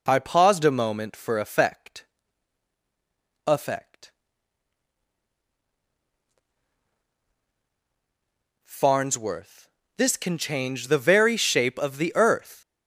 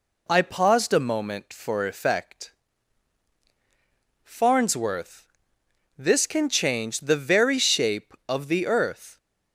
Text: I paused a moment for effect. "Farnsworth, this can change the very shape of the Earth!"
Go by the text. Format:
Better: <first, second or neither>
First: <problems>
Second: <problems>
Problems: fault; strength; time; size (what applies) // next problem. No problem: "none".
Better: second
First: says "effect" twice; at 3.4 s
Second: none